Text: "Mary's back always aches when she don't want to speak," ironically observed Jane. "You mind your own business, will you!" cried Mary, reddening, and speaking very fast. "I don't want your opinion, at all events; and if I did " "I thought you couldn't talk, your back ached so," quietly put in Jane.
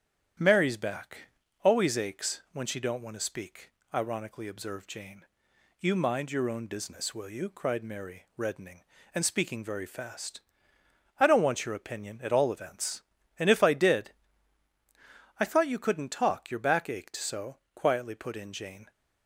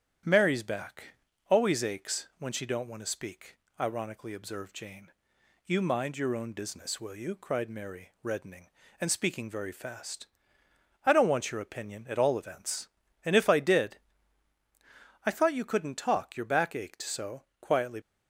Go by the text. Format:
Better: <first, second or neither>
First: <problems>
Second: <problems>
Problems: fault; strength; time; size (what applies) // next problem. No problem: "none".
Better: first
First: starts louder than the rest; strong; until 1.7 s; 9.5 dB // pauses between "back" and "always"; slight; at 1.2 s; 0.34 s long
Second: starts louder than the rest; strong; until 1.5 s; 9.5 dB // pauses between "back" and "always"; slight; at 1.1 s; 0.34 s long // stops before "put in Jane"; at 18.0 s